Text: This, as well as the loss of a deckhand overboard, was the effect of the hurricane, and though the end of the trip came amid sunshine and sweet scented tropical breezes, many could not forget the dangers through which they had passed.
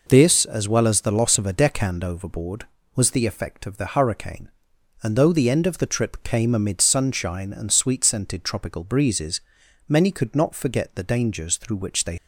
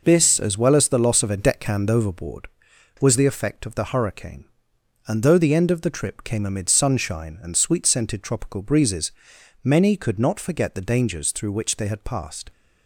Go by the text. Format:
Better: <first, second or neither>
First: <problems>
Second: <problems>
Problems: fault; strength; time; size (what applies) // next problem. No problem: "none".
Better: second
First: stops before "had passed"; at 12.1 s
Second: none